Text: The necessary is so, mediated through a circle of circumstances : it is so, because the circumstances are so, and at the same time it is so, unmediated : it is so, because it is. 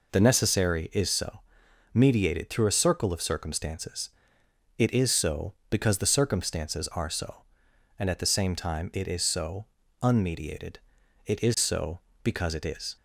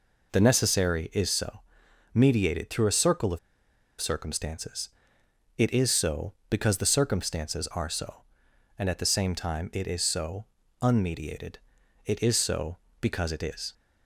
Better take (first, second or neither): first